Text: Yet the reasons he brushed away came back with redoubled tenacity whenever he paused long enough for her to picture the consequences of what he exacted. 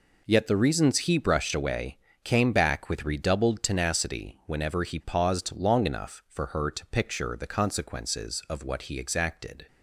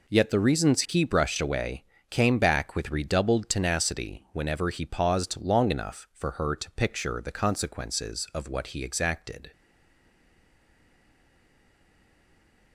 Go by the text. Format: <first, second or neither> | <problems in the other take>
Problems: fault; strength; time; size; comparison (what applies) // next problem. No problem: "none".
first | pauses between "away" and "came"; slight; at 1.8 s; 0.26 s long; slight in the first // stays silent after the last word; strong; from 9.5 s on; 3.2 s long